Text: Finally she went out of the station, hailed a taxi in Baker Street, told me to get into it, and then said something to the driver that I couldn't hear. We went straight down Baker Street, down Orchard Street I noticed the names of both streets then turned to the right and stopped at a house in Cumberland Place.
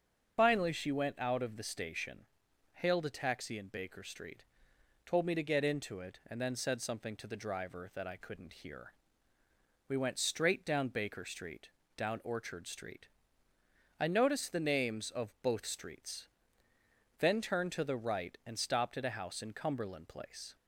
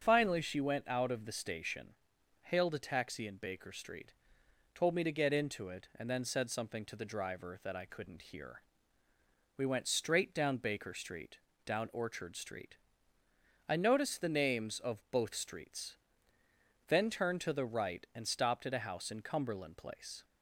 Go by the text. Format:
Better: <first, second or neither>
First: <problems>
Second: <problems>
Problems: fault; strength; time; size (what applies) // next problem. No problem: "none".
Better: second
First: loses the start of "Finally"; at 0.3 s; 55 ms // starts louder than the rest; until 1.4 s; 6.5 dB // pauses between "Street" and "I"; noticeable; at 13.0 s; 0.94 s long // pauses between "streets" and "then"; noticeable; at 16.2 s; 0.94 s long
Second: starts louder than the rest; until 1.0 s; 6.5 dB // pauses between "Street" and "I"; noticeable; at 12.7 s; 0.94 s long // pauses between "streets" and "then"; noticeable; at 15.9 s; 0.94 s long